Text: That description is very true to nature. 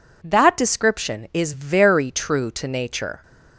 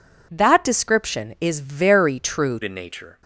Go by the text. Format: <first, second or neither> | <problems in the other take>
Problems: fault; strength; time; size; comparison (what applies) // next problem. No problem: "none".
first | changes voice at "to"; from 2.6 s on; 0.6 s long